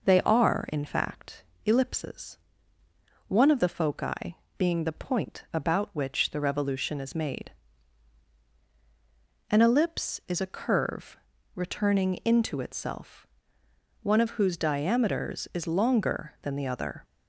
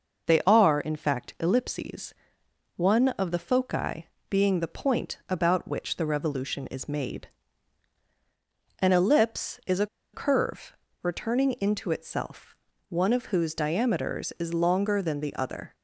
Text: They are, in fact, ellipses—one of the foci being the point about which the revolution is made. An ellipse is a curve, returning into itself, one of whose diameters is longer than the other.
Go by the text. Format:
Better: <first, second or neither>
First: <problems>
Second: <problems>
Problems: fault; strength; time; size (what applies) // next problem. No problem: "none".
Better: first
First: pauses between "foci" and "being"; slight; at 4.3 s; 0.20 s long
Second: pauses between "foci" and "being"; slight; at 4.0 s; 0.22 s long // pauses between "a" and "curve"; slight; at 9.8 s; 0.28 s long